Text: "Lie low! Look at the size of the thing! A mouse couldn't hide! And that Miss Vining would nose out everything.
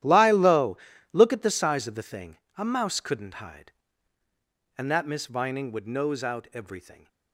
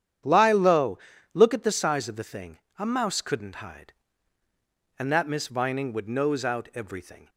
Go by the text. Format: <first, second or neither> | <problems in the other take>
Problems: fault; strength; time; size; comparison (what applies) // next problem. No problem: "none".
second | gets quieter; strong; throughout; 15.5 dB // starts louder than the rest; strong; until 1.3 s; 12 dB; strong in the second